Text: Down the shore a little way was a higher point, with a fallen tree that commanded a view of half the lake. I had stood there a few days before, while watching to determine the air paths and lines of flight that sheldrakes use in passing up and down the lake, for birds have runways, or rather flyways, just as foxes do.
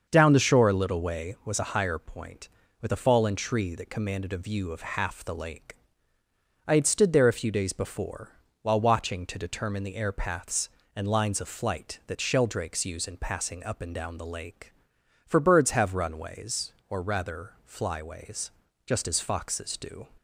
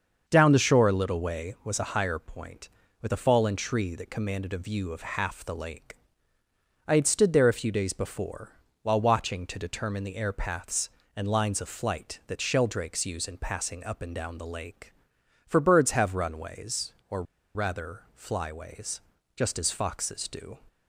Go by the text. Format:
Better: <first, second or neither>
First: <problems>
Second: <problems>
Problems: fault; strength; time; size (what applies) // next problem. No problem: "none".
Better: first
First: starts louder than the rest; until 1.1 s; 6.5 dB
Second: starts louder than the rest; until 1.2 s; 6.5 dB // pauses between "or" and "rather"; slight; at 17.2 s; 0.32 s long